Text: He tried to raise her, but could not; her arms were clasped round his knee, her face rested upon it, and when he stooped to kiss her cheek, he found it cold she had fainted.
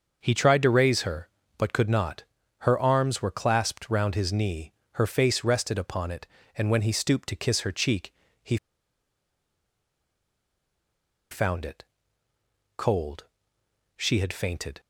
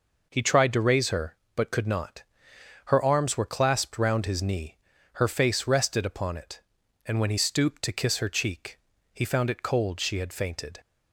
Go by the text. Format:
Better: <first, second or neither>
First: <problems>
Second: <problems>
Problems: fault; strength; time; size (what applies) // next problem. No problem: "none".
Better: second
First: starts louder than the rest; noticeable; until 1.2 s; 6 dB // pauses between "he" and "found"; strong; at 8.5 s; 2.7 s long // pauses between "it" and "cold"; noticeable; at 11.8 s; 0.94 s long // pauses between "cold" and "she"; noticeable; at 13.2 s; 0.72 s long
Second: none